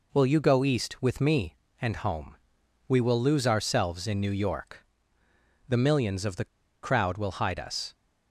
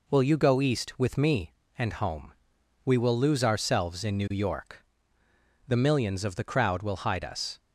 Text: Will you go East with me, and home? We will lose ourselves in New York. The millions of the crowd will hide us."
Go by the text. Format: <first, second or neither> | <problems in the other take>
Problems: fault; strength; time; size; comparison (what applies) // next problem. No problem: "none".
second | pauses between "the" and "crowd"; slight; at 6.4 s; 0.35 s long